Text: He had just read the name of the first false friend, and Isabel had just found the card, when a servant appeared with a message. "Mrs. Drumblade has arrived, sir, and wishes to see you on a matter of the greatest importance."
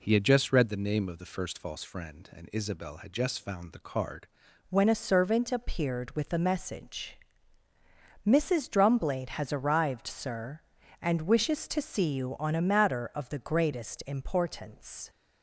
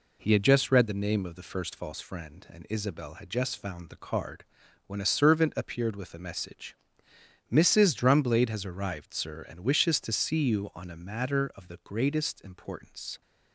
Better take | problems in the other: second | changes voice at "when"; from 4.6 s on; 10.4 s long

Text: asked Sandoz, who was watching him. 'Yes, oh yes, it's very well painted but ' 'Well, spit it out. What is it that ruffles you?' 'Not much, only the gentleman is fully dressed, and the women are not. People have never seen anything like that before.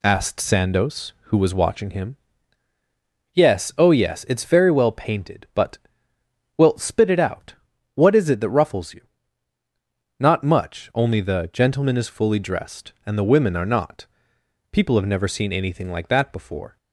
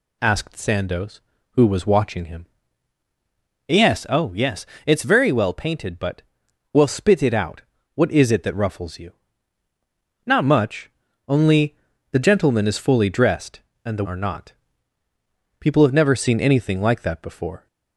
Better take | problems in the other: first | pauses between "only" and "the"; slight; at 11.7 s; 0.36 s long // skips "women"; at 14.0 s

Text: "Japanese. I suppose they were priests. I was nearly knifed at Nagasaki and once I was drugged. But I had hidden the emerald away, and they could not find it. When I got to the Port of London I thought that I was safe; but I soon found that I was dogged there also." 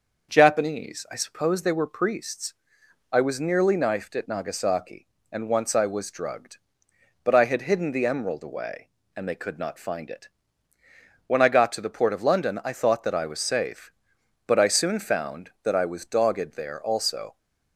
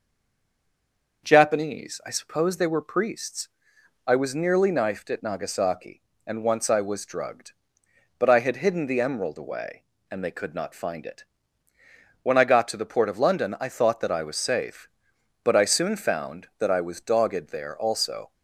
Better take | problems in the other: first | stays silent before the first word; noticeable; until 1.2 s; 1.2 s long // starts louder than the rest; noticeable; until 2.2 s; 6 dB; noticeable in the first

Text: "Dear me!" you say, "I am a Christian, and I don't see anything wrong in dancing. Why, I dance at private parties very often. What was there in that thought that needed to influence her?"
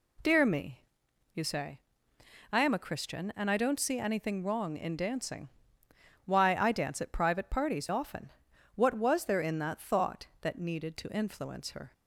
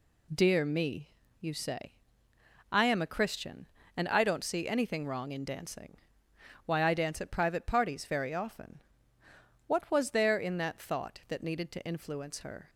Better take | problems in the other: second | skips "very"; at 7.8 s

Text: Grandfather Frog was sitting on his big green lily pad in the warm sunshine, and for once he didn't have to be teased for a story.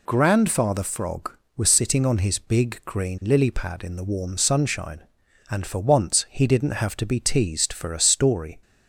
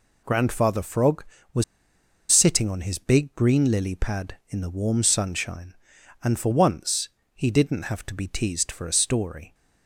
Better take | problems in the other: first | pauses between "was" and "sitting"; noticeable; at 1.6 s; 0.68 s long // pauses between "once" and "he"; slight; at 7.0 s; 0.24 s long

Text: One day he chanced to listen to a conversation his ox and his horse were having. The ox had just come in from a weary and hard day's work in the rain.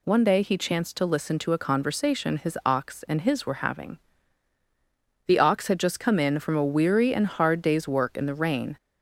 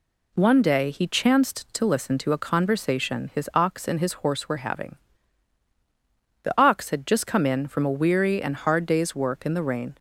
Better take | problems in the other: second | skips "horse"; at 3.4 s

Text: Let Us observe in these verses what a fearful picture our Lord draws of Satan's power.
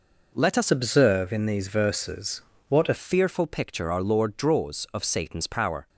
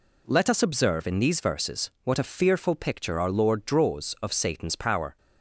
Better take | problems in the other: second | changes voice from "observe" to "a"; from 0.6 to 2.9 s; 2.3 s long // pauses between "verses" and "what"; slight; at 2.4 s; 0.26 s long

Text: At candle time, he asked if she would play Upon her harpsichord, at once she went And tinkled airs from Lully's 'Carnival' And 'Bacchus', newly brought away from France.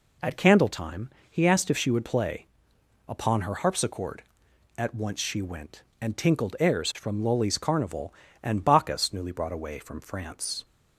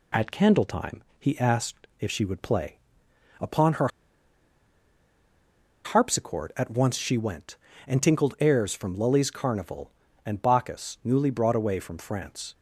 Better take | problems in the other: first | pauses between "play" and "Upon"; noticeable; at 2.7 s; 0.64 s long; noticeable in the first // pauses between "her" and "harpsichord"; strong; at 3.8 s; 1.9 s long

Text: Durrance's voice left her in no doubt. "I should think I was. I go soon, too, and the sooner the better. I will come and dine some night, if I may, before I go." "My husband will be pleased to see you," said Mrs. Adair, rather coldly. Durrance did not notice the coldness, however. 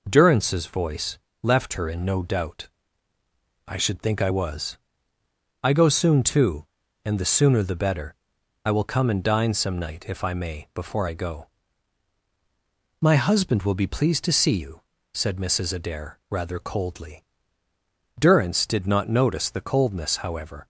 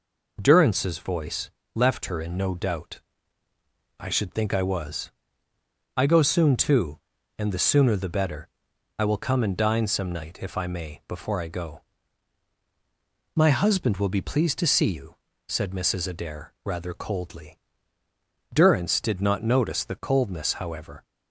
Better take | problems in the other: neither | pauses between "voice" and "left"; slight; the same in both

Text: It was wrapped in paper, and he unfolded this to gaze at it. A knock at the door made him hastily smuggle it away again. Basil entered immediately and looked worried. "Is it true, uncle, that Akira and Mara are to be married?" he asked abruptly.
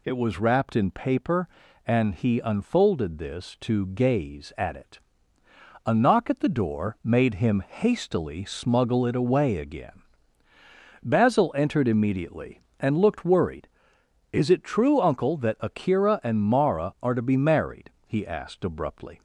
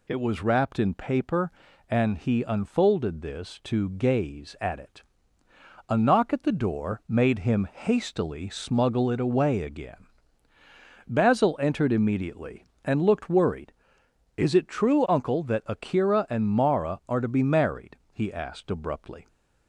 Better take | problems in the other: neither | none

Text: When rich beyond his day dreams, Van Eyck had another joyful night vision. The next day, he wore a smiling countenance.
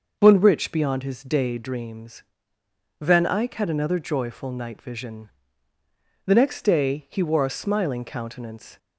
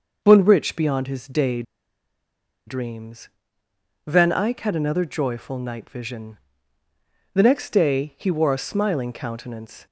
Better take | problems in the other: first | pauses between "day" and "dreams"; at 1.6 s; 1.0 s long

